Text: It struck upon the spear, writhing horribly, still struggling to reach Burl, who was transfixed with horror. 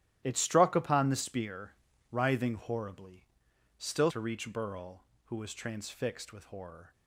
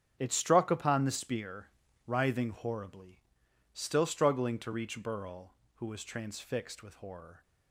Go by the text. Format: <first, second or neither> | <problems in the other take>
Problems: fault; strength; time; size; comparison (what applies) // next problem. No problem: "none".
second | starts louder than the rest; strong; until 1.2 s; 13.5 dB; strong in the second // skips "struggling"; at 4.1 s